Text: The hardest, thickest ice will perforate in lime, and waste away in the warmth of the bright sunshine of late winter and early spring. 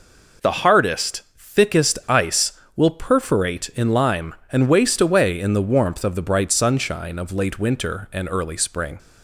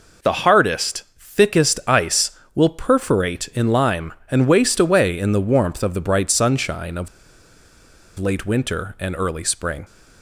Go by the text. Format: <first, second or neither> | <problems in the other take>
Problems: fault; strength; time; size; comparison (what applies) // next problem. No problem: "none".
first | pauses between "of" and "late"; at 7.0 s; 1.1 s long